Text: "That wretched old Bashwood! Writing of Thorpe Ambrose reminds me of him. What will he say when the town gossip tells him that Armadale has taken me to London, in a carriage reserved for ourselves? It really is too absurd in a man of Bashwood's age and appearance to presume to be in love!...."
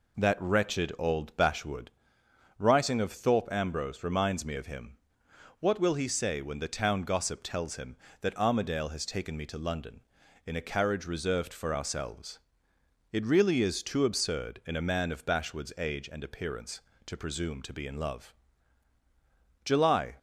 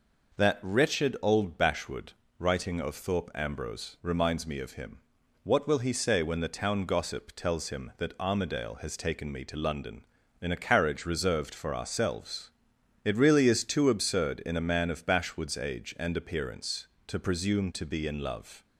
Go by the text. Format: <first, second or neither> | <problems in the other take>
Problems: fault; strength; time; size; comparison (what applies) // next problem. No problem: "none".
second | goes on to say "July"; from 19.6 s on; 0.50 s long